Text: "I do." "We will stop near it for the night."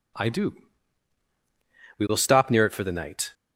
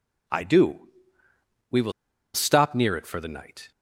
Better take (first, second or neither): first